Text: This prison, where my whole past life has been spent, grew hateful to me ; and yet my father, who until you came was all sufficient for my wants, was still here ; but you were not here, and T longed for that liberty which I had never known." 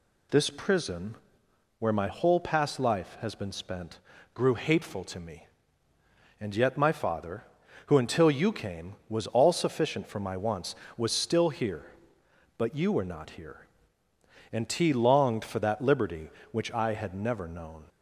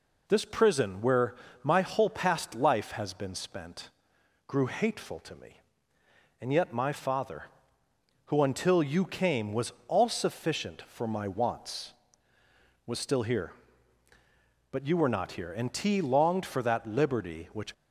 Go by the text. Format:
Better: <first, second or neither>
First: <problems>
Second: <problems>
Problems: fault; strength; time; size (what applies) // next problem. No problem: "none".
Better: first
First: none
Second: pauses between "where" and "my"; slight; at 1.3 s; 0.28 s long // pauses between "was" and "all"; slight; at 9.7 s; 0.16 s long // stops before "I had never known"; at 17.7 s